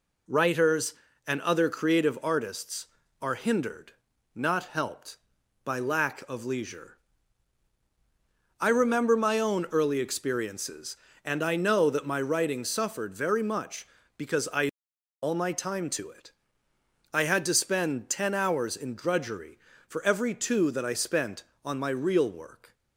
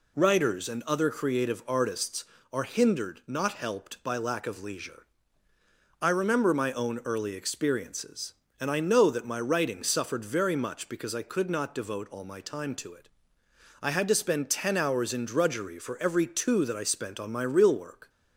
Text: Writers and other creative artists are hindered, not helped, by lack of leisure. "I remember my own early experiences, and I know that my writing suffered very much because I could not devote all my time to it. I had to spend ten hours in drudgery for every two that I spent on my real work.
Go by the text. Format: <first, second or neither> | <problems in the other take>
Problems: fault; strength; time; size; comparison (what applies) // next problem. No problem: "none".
second | skips "could not devote"; at 14.9 s